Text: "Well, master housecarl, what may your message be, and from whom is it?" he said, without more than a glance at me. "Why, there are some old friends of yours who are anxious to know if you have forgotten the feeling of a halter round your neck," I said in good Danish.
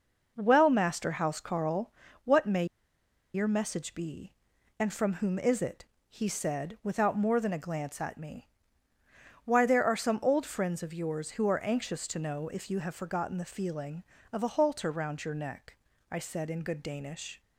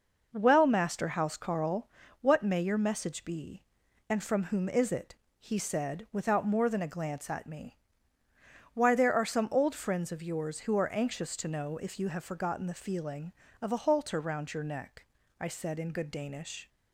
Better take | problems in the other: second | pauses between "may" and "your"; noticeable; at 2.6 s; 0.70 s long

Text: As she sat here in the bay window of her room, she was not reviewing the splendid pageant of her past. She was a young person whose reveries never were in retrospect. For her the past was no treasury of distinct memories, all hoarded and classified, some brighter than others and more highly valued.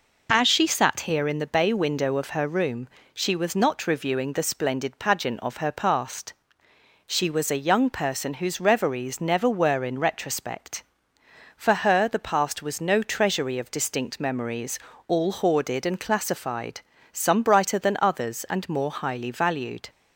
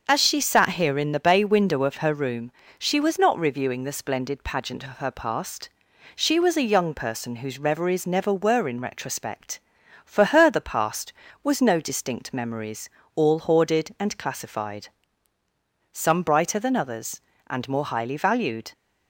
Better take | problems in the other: first | starts louder than the rest; until 1.0 s; 6.5 dB // skips "treasury of"; at 11.7 s

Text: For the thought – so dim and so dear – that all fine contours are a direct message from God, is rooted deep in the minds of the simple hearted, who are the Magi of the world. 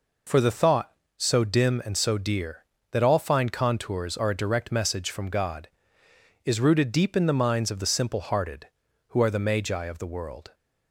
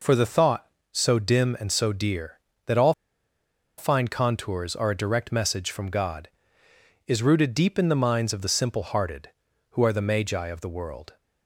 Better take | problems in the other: first | pauses between "all" and "fine"; noticeable; at 2.9 s; 0.85 s long

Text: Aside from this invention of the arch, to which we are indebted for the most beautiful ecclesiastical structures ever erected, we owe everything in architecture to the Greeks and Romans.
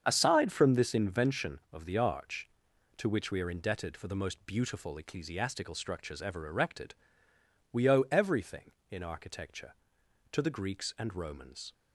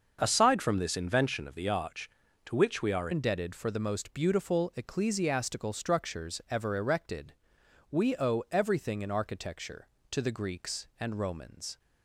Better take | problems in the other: first | starts louder than the rest; until 1.2 s; 6.5 dB; strong in the first // changes voice at "indebted"; from 3.1 s on; 8.6 s long

